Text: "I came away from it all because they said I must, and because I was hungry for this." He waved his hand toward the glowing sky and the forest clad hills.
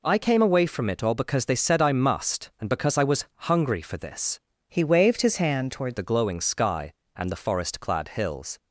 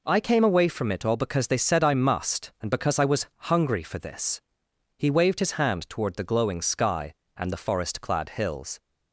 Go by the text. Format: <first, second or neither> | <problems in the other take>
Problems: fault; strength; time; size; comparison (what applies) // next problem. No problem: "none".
second | pauses between "was" and "hungry"; slight; at 3.2 s; 0.24 s long; slight in the second // changes voice from "He" to "toward"; from 4.6 to 5.9 s; 1.3 s long